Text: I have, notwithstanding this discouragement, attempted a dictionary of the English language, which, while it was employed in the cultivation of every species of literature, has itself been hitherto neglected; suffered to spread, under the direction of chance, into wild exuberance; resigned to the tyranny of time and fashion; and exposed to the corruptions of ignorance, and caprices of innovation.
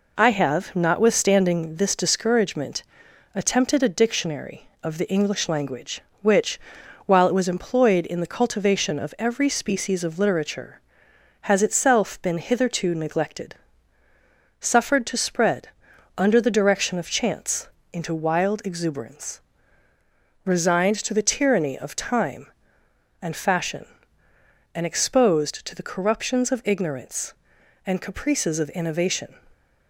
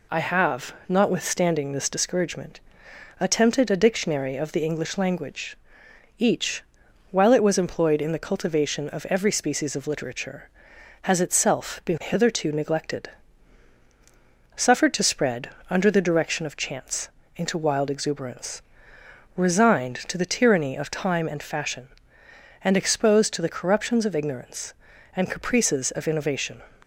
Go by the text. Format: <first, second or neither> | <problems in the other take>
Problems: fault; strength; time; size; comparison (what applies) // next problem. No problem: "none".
first | says "each" for "which"; at 6.1 s